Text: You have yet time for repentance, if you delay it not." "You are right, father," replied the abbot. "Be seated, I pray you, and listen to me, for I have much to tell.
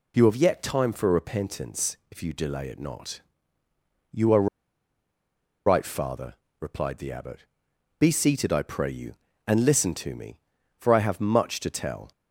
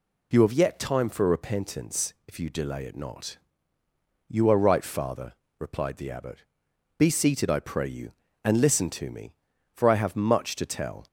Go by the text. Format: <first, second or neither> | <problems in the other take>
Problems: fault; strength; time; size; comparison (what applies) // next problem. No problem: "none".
second | pauses between "are" and "right"; at 4.4 s; 1.2 s long